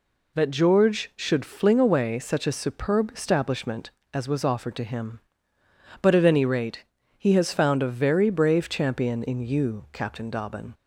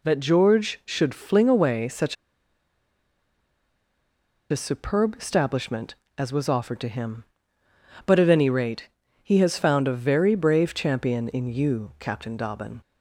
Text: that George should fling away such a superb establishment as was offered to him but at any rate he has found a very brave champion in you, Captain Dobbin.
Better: first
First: pauses between "rate" and "he"; slight; at 6.8 s; 0.35 s long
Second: pauses between "such" and "a"; strong; at 2.1 s; 2.3 s long // pauses between "rate" and "he"; slight; at 8.8 s; 0.36 s long

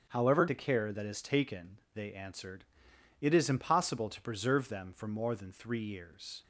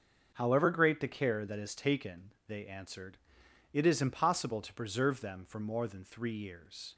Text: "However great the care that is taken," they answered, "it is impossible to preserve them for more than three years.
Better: second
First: starts louder than the rest; strong; until 1.1 s; 7.5 dB // skips "great"; at 0.4 s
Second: starts louder than the rest; until 1.3 s; 6.5 dB

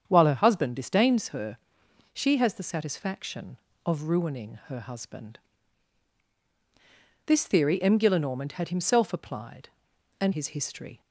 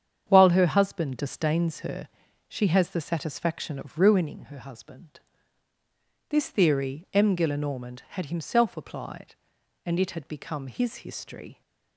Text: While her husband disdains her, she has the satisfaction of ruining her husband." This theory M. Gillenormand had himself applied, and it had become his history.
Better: second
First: starts louder than the rest; strong; until 1.0 s; 8 dB // skips "it had become"; at 10.3 s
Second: starts louder than the rest; strong; until 1.3 s; 8 dB

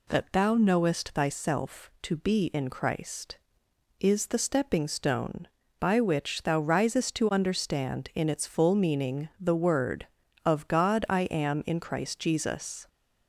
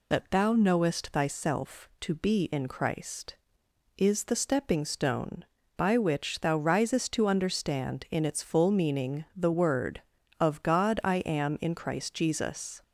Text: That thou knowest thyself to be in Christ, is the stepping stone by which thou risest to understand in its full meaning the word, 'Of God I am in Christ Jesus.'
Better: first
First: none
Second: loses the start of "That"; at 0.1 s; 50 ms

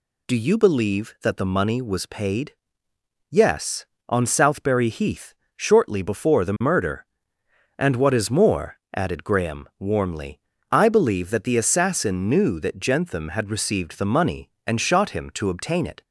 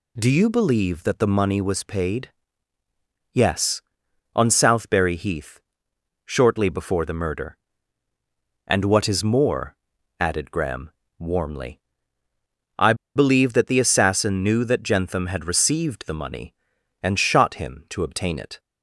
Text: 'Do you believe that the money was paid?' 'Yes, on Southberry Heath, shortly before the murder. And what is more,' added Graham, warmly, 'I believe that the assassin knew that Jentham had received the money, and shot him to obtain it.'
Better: first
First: none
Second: pauses between "I" and "believe"; slight; at 12.9 s; 0.21 s long

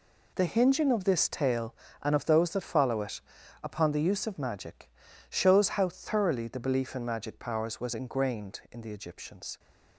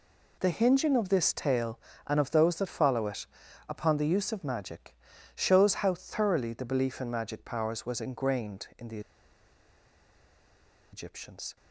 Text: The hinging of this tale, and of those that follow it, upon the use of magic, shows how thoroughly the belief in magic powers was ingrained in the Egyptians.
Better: first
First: none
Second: pauses between "the" and "Egyptians"; strong; at 8.9 s; 1.9 s long

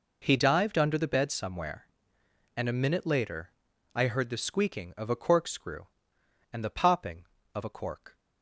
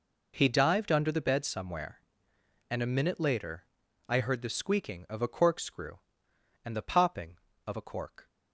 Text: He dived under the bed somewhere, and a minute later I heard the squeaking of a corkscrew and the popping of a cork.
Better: neither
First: pauses between "later" and "I"; noticeable; at 3.4 s; 0.46 s long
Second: pauses between "later" and "I"; noticeable; at 3.6 s; 0.46 s long

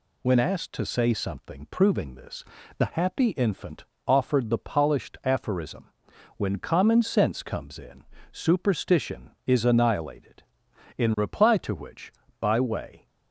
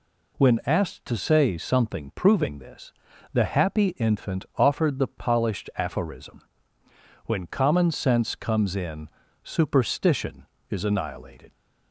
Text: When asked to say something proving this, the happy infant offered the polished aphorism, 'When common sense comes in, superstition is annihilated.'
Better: second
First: pauses between "infant" and "offered"; slight; at 3.8 s; 0.22 s long // goes on to say "In reply to which by way"; strong; from 10.9 s on; 2.0 s long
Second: none

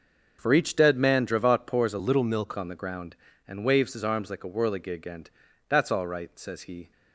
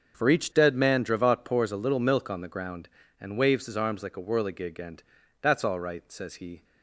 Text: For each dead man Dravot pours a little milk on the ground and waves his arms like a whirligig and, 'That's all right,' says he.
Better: second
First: starts louder than the rest; until 1.4 s; 6.5 dB // changes voice from "little" to "milk"; from 1.9 to 2.5 s; 0.6 s long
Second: starts louder than the rest; until 1.2 s; 7 dB

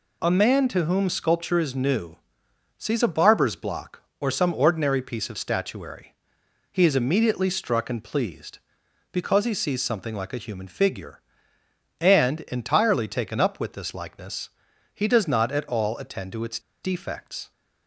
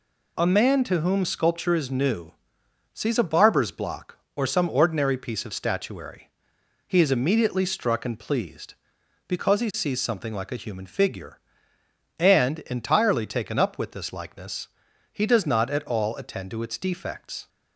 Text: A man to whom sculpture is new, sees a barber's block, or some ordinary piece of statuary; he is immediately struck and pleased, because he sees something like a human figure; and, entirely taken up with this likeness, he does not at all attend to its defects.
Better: second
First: pauses between "its" and "defects"; slight; at 16.5 s; 0.23 s long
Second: none

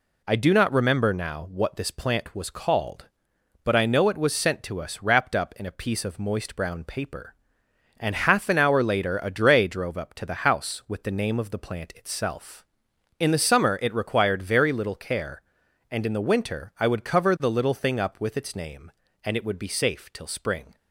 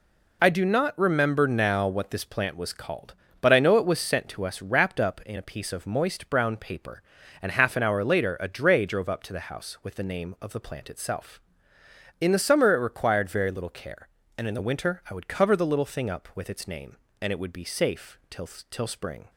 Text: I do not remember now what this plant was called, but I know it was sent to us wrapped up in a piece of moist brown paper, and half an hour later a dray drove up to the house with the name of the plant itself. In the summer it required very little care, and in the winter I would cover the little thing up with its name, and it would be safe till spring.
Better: first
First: none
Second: says "till" twice; at 18.6 s

